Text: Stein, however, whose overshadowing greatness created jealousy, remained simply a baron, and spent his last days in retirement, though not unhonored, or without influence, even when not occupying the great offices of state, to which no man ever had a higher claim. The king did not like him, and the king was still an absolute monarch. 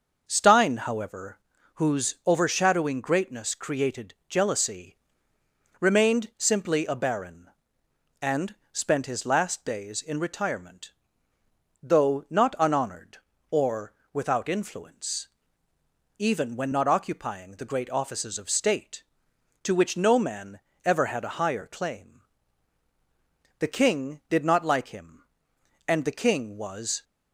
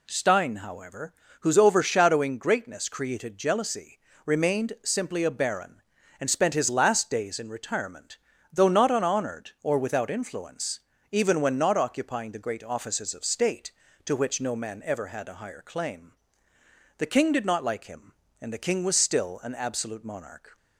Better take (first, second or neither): second